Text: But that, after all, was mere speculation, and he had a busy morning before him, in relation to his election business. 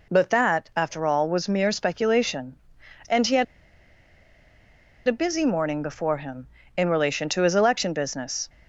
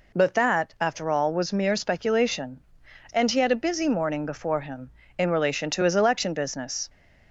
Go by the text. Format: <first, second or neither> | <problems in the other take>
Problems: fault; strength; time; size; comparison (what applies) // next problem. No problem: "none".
second | pauses between "had" and "a"; strong; at 3.4 s; 1.6 s long